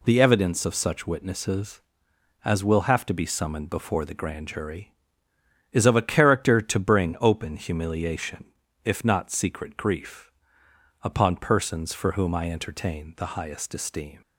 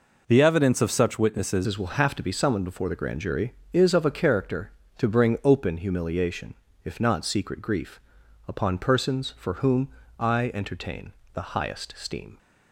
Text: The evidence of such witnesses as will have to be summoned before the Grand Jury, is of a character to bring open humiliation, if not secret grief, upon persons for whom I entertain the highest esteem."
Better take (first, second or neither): first